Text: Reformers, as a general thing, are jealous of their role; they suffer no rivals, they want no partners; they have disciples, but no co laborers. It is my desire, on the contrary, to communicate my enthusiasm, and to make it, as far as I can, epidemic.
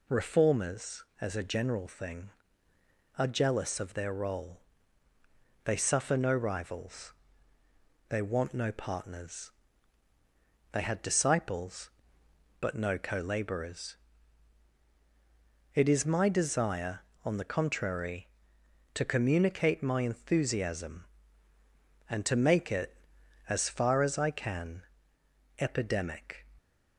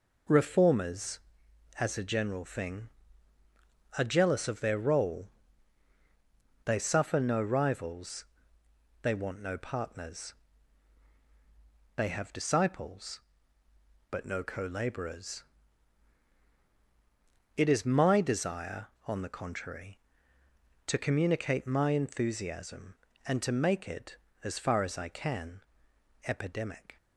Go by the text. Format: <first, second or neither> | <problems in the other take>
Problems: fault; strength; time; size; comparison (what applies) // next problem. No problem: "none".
second | says "had" for "have"; at 10.8 s